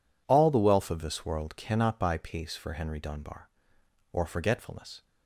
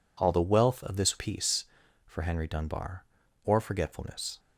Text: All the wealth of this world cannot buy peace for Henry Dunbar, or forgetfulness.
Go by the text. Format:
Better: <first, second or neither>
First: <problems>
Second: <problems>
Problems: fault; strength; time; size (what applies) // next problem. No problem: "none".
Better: first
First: none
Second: skips "world cannot buy"; at 1.1 s